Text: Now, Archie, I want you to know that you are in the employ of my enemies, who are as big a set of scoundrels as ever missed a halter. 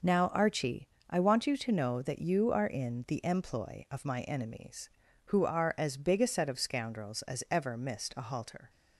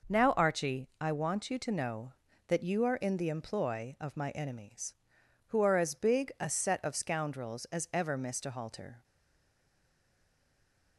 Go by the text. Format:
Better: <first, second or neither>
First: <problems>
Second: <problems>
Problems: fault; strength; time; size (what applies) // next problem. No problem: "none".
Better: first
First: none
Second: stays silent after the last word; noticeable; from 9.0 s on; 1.9 s long